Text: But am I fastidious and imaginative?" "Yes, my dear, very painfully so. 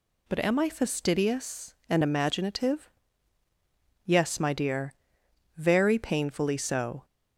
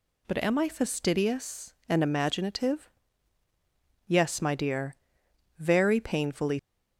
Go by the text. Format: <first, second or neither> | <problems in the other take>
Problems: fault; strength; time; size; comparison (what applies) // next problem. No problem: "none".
first | stops before "so"; at 6.5 s